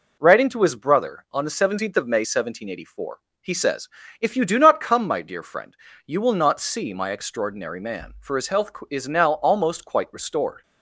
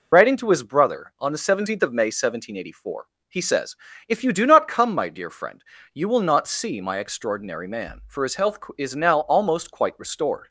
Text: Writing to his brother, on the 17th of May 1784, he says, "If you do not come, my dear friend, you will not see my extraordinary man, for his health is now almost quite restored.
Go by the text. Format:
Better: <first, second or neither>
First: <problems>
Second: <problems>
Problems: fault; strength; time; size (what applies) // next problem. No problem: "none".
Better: first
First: none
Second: loses the start of "Writing"; at 0.1 s; 50 ms